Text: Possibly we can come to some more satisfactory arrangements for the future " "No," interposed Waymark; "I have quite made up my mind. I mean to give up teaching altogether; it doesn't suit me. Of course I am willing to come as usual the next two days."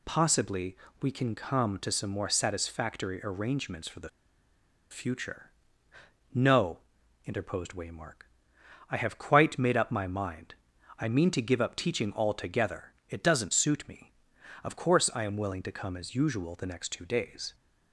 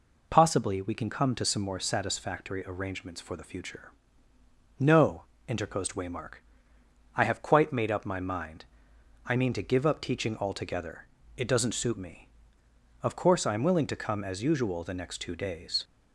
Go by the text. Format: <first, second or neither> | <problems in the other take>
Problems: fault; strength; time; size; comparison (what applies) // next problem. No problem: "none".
second | pauses between "Possibly" and "we"; slight; at 0.7 s; 0.26 s long // pauses between "the" and "future"; noticeable; at 4.0 s; 0.82 s long